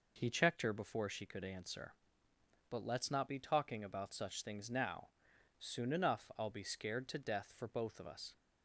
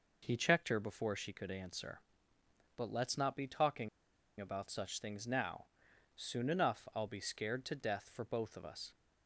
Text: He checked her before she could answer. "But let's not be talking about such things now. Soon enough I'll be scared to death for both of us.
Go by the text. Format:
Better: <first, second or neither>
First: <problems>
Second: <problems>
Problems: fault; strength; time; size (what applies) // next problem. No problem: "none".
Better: first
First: none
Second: pauses between "talking" and "about"; noticeable; at 3.8 s; 0.51 s long